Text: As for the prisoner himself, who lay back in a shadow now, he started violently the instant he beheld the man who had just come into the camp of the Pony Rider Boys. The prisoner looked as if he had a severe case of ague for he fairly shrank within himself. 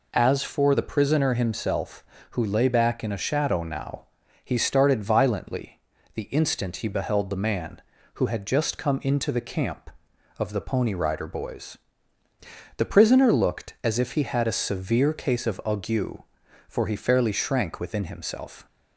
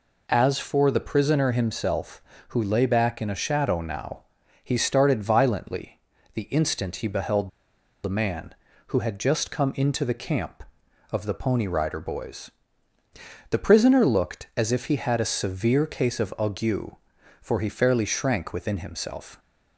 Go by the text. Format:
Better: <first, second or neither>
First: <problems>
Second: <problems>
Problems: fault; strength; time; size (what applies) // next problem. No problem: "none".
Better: first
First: pauses between "violently" and "the"; slight; at 5.7 s; 0.34 s long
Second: pauses between "violently" and "the"; slight; at 5.9 s; 0.34 s long // pauses between "beheld" and "the"; noticeable; at 7.4 s; 0.54 s long